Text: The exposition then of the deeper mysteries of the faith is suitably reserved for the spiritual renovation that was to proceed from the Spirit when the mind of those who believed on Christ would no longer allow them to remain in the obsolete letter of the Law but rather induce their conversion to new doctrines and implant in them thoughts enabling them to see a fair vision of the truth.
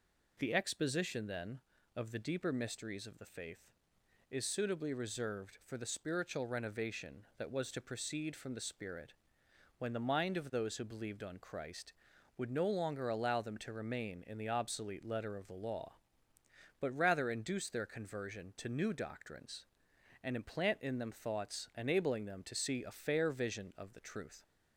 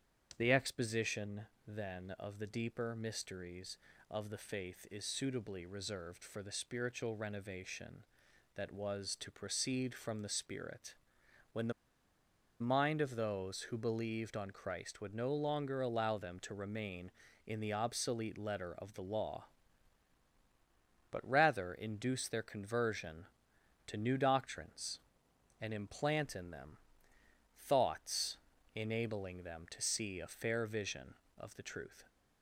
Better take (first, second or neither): first